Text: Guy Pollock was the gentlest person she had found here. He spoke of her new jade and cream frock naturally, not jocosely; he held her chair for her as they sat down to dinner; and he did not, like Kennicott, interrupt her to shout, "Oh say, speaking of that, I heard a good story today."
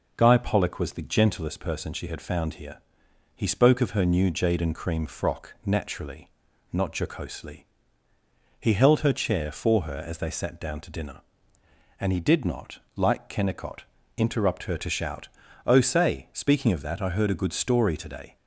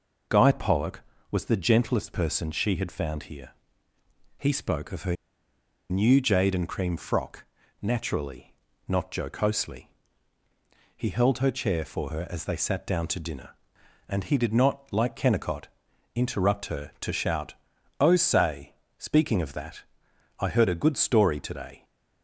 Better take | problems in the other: first | pauses between "her" and "new"; noticeable; at 5.1 s; 0.74 s long // pauses between "frock" and "naturally"; at 7.4 s; 0.40 s long

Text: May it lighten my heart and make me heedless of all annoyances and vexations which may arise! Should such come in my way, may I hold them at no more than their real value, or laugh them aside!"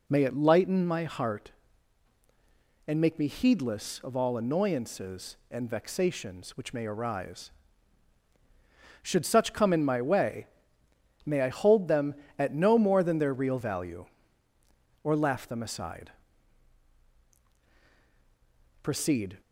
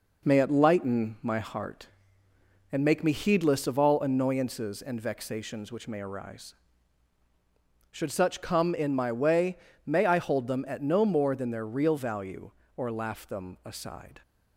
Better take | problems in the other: second | goes on to say "Proceed"; from 18.8 s on; 0.56 s long

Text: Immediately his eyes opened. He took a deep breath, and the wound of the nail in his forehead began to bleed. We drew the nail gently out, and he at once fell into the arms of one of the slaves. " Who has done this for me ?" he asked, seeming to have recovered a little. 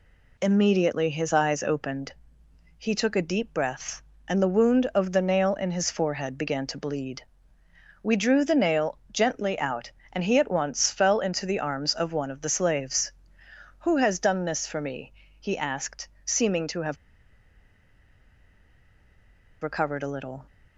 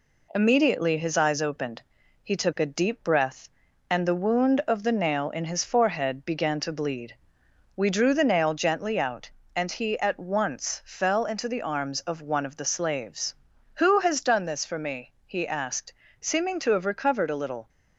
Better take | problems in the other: second | pauses between "have" and "recovered"; strong; at 16.9 s; 2.6 s long

